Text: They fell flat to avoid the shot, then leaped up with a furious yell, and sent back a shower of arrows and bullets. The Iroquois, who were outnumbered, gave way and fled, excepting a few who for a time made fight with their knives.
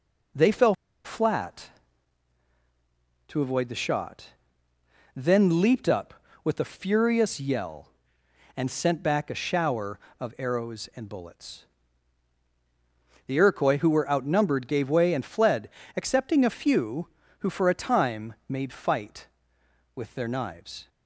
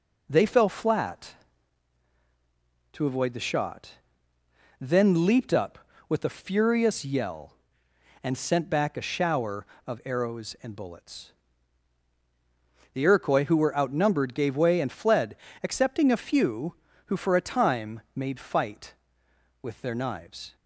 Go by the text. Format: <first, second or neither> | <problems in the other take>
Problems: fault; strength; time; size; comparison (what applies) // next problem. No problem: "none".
second | pauses between "fell" and "flat"; slight; at 0.7 s; 0.29 s long